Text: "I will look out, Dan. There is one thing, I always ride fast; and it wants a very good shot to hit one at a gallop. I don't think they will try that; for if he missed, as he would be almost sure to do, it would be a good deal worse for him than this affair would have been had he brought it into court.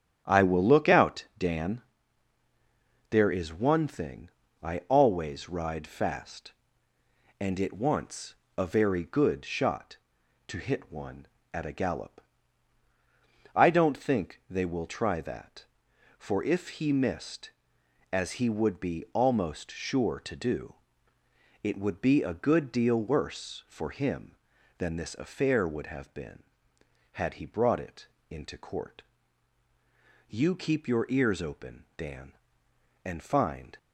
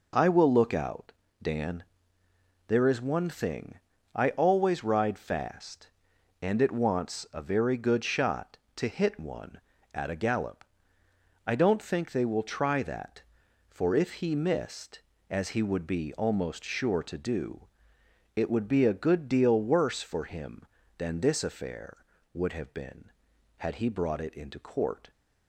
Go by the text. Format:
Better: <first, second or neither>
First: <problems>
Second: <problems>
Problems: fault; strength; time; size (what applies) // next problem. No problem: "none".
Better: second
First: starts louder than the rest; strong; until 1.2 s; 10 dB // pauses between "wants" and "a"; slight; at 8.3 s; 0.24 s long // pauses between "it" and "into"; slight; at 28.0 s; 0.22 s long // goes on to say "You keep your ears open Dan and find"; strong; from 30.2 s on; 3.5 s long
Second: none